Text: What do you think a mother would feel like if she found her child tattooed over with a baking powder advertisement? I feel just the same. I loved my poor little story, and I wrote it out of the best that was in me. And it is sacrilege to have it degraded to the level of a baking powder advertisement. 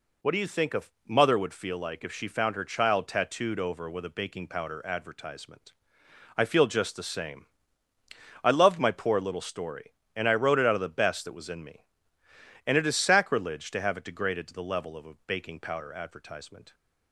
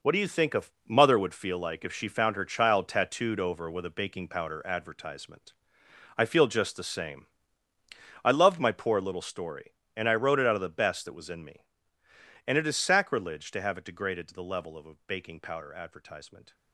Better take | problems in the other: first | gets quieter; strong; throughout; 10.5 dB // pauses between "a" and "mother"; slight; at 0.6 s; 0.24 s long; slight in the first

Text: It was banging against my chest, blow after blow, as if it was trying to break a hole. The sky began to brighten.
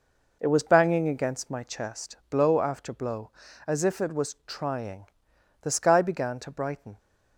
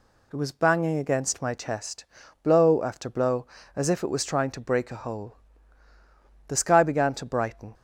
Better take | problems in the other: second | skips "to break a hole"; at 5.3 s

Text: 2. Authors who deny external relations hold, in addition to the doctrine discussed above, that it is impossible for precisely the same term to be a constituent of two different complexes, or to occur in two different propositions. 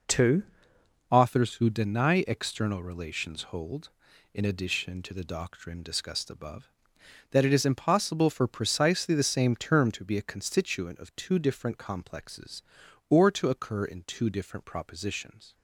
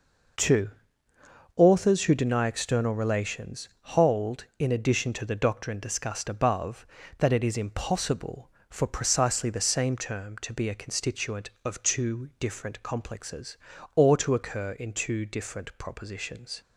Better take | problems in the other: second | changes voice at "Authors"; from 1.0 s on; 14.5 s long

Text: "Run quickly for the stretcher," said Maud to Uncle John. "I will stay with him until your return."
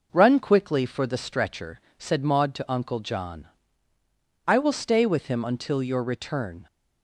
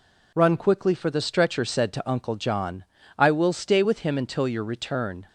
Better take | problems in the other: first | skips "Maud"; at 1.9 s

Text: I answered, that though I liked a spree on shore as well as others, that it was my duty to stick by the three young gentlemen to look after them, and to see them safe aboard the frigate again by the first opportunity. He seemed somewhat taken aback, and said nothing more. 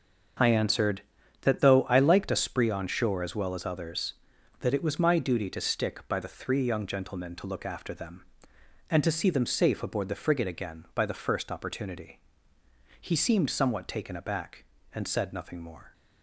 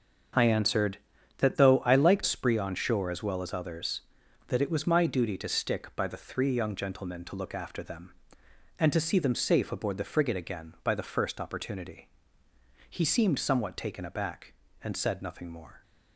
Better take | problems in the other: first | starts louder than the rest; until 1.7 s; 6.5 dB; also in the first // skips "a"; at 2.2 s

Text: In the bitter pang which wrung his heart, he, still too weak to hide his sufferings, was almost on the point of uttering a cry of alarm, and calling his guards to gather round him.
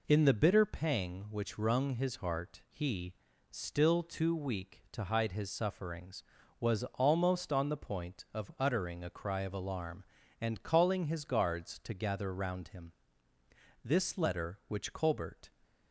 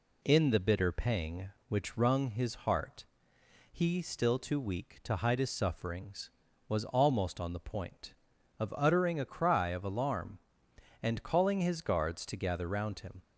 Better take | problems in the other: second | goes on to say "This letter which Colbert"; from 13.8 s on; 1.6 s long

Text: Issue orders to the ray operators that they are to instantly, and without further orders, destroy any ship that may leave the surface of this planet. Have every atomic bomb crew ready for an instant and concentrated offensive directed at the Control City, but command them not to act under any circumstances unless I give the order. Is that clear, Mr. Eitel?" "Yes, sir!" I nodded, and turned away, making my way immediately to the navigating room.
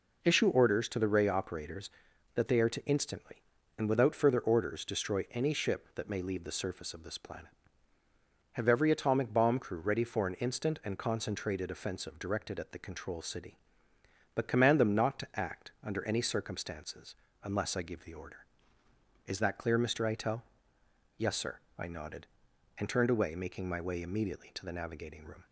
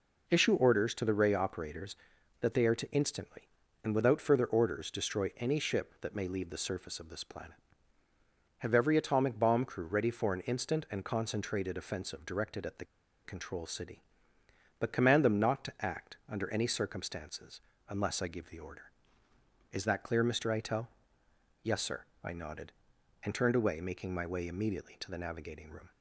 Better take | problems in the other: first | pauses between "the" and "Control"; at 12.8 s; 0.39 s long // pauses between "circumstances" and "unless"; slight; at 17.6 s; 0.26 s long; slight in the first

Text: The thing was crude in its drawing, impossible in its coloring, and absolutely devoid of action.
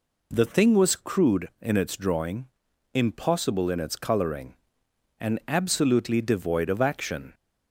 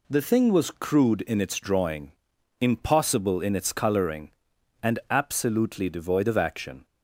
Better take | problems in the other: neither | none

